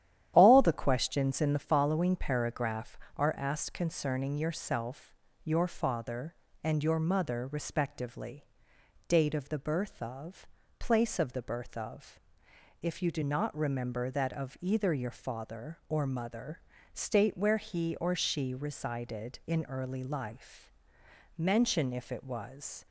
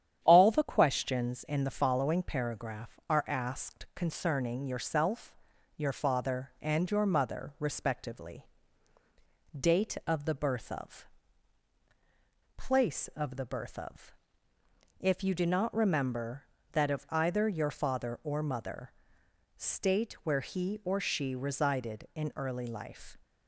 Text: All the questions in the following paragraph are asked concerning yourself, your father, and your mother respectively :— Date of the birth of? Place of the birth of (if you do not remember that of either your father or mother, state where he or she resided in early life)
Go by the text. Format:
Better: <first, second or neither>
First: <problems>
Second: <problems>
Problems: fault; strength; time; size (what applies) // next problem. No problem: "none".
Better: second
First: starts louder than the rest; strong; until 1.3 s; 11 dB // goes on to say "Mention if it was"; from 21.3 s on; 1.4 s long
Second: starts louder than the rest; strong; until 1.2 s; 9.5 dB